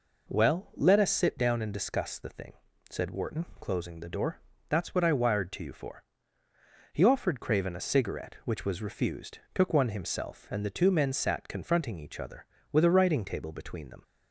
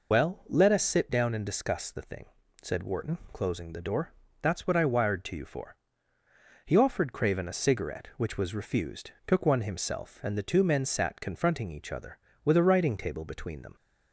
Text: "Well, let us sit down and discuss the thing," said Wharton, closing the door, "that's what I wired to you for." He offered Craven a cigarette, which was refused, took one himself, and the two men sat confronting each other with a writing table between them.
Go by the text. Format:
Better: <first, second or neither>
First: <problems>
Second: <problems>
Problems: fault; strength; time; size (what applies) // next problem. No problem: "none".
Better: first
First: none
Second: loses the start of "Well"; at 0.1 s; 95 ms